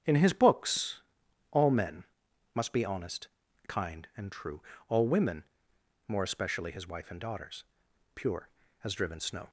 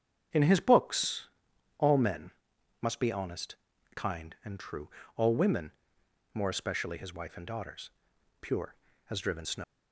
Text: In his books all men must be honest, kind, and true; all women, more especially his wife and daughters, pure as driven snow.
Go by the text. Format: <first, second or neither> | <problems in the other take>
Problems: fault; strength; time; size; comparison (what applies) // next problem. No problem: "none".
first | starts louder than the rest; strong; until 1.8 s; 7.5 dB; strong in the first // pauses between "books" and "all"; noticeable; at 1.2 s; 0.50 s long; noticeable in the first // pauses between "men" and "must"; noticeable; at 2.3 s; 0.50 s long; noticeable in the first // leaves "snow" unfinished; at 9.6 s; 100 ms